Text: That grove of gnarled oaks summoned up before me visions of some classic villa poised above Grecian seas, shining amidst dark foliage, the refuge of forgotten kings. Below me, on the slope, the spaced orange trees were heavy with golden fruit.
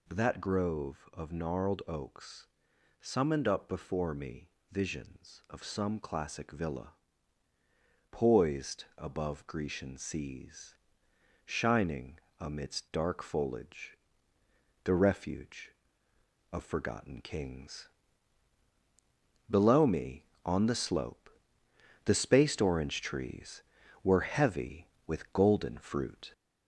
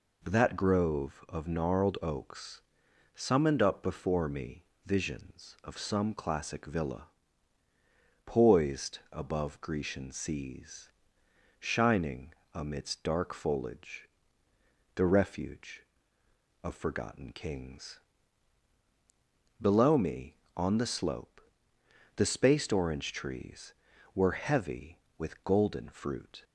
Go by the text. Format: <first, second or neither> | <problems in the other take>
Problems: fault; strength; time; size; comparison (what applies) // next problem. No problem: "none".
second | gets louder; slight; throughout; 2.5 dB // pauses between "oaks" and "summoned"; noticeable; at 2.4 s; 0.54 s long; noticeable in the second // pauses between "me" and "visions"; slight; at 4.4 s; 0.22 s long; slight in the second // pauses between "villa" and "poised"; at 6.9 s; 1.1 s long; also in the second // pauses between "shining" and "amidst"; slight; at 12.1 s; 0.20 s long; slight in the second